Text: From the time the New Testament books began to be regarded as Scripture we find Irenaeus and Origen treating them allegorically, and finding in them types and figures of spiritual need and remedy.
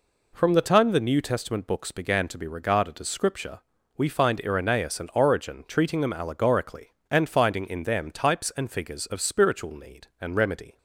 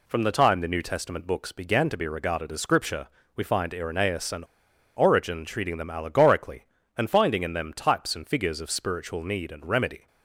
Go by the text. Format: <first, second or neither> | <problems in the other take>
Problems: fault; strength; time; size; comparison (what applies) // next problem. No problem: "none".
first | pauses between "Scripture" and "we"; slight; at 3.0 s; 0.26 s long; slight in the first // pauses between "and" and "Origen"; noticeable; at 4.4 s; 0.52 s long